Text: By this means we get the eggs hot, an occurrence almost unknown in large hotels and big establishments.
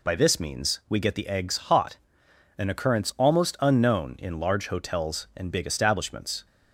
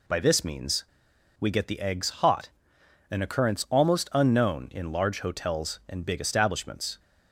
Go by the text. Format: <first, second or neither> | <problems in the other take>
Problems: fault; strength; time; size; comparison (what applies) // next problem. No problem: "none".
first | pauses between "means" and "we"; noticeable; at 0.8 s; 0.54 s long